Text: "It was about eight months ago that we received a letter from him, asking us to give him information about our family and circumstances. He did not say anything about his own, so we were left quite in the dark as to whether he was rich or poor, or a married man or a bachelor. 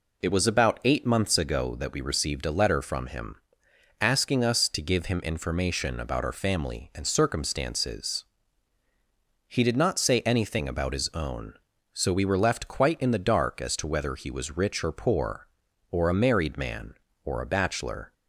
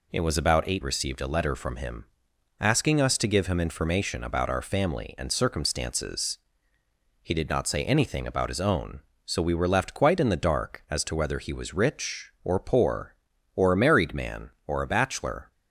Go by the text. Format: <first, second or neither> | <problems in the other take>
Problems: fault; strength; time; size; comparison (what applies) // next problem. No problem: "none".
first | skips "months ago that we"; at 0.8 s